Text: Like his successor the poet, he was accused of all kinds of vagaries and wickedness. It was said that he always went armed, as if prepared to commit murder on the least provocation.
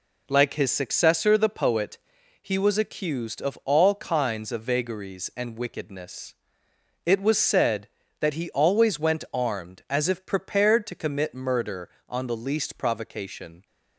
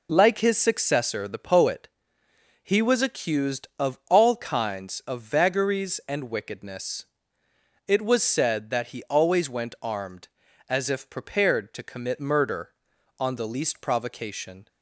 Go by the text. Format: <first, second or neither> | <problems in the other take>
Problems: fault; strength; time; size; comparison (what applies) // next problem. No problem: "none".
neither | none